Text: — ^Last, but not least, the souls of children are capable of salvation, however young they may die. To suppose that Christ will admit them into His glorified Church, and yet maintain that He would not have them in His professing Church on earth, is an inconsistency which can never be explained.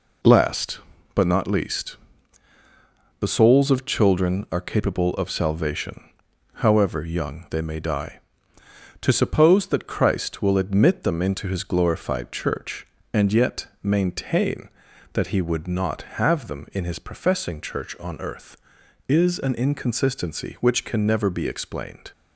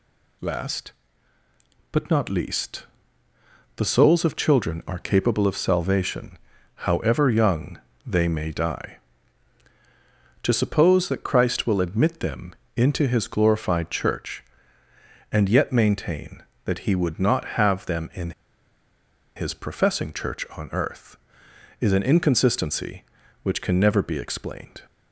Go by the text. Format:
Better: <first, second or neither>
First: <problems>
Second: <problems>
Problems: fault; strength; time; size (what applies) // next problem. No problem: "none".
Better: first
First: none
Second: pauses between "young" and "they"; slight; at 7.7 s; 0.30 s long // pauses between "them" and "into"; slight; at 12.5 s; 0.22 s long // pauses between "in" and "His"; at 18.3 s; 1.0 s long